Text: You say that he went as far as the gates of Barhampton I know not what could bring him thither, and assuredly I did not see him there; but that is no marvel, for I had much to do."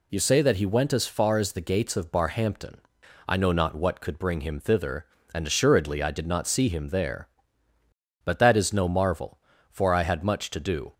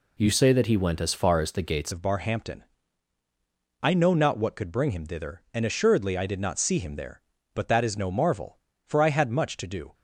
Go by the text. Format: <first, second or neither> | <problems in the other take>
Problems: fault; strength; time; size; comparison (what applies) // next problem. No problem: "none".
first | changes voice at "of"; from 1.9 s on; 8.0 s long // pauses between "Barhampton" and "I"; at 2.6 s; 1.2 s long; noticeable in the first